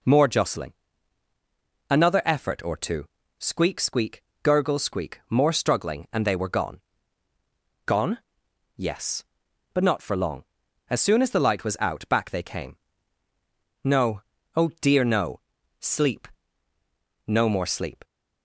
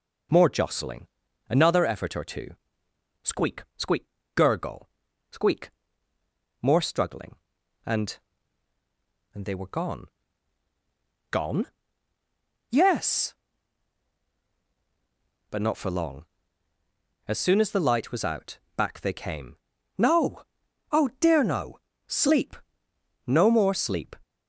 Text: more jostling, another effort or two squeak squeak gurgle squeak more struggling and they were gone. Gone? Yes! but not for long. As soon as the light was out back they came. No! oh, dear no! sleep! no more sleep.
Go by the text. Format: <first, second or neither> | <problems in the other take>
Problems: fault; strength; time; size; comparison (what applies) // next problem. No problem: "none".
first | pauses between "two" and "squeak"; noticeable; at 2.5 s; 0.68 s long; slight in the first // pauses between "squeak" and "gurgle"; slight; at 4.0 s; 0.30 s long; slight in the first // pauses between "gurgle" and "squeak"; at 4.8 s; 0.42 s long // pauses between "squeak" and "more"; noticeable; at 5.6 s; 0.94 s long // says "and" twice; at 9.3 s // pauses between "out" and "back"; slight; at 18.5 s; 0.18 s long